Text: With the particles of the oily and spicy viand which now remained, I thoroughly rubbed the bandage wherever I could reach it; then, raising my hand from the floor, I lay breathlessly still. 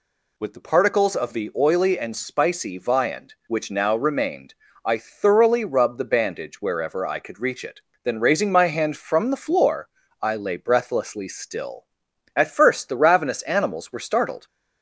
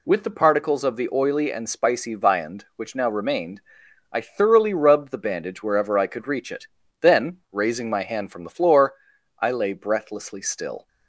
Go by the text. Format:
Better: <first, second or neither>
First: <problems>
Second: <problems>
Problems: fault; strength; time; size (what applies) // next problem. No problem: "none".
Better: second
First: goes on to say "At first the ravenous animals were startled"; strong; from 12.3 s on; 2.1 s long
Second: none